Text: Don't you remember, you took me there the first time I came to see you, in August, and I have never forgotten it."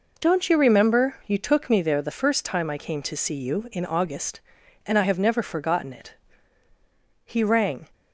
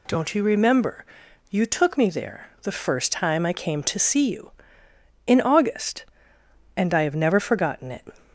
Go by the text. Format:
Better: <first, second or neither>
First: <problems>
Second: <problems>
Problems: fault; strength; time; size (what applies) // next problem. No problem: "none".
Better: second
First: goes on to say "He rang"; noticeable; from 7.2 s on; 0.64 s long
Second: none